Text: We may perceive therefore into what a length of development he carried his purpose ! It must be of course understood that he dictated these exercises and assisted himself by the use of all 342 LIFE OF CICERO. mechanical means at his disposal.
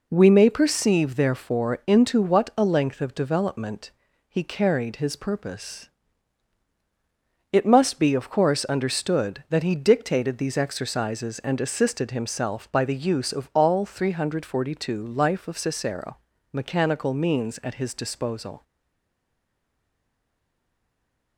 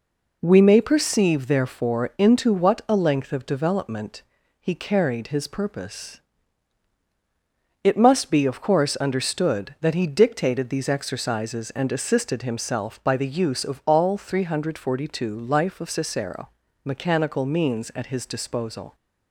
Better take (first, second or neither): second